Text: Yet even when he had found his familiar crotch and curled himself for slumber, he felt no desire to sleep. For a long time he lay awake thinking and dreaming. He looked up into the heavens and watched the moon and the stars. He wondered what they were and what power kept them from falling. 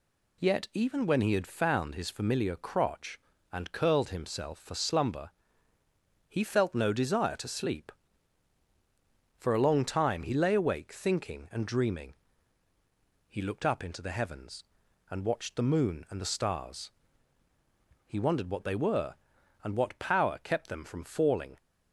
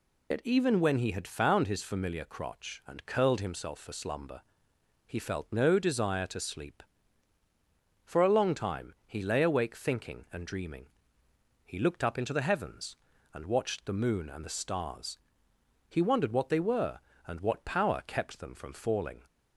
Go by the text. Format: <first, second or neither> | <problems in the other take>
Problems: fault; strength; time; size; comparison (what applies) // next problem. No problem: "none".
first | loses the start of "Yet"; at 0.3 s; 55 ms